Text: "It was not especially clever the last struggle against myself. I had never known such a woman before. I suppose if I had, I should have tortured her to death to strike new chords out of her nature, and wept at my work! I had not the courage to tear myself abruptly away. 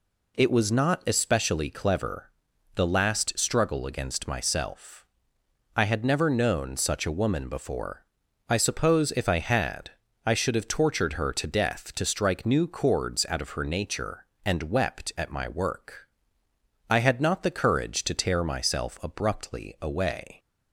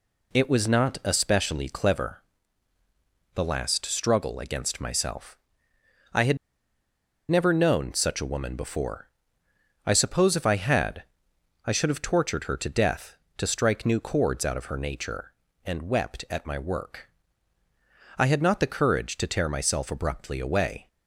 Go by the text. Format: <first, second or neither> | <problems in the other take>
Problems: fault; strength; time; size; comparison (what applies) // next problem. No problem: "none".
first | pauses between "clever" and "the"; at 2.2 s; 1.1 s long; noticeable in the first // pauses between "had" and "never"; noticeable; at 6.3 s; 0.92 s long